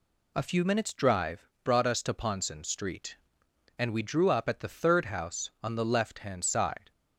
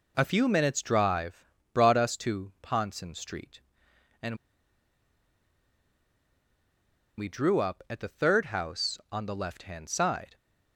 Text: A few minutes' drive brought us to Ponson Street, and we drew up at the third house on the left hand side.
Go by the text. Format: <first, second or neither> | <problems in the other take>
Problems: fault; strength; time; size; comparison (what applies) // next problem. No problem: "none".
first | pauses between "drive" and "brought"; slight; at 1.4 s; 0.30 s long; slight in the first // pauses between "and" and "we"; strong; at 4.3 s; 2.8 s long